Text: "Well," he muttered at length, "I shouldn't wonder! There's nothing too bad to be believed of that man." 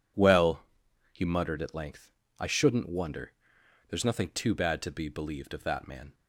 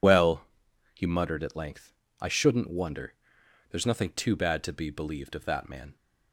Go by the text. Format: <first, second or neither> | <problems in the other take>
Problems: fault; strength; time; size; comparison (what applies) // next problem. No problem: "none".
first | loses the start of "Well"; at 0.0 s; 55 ms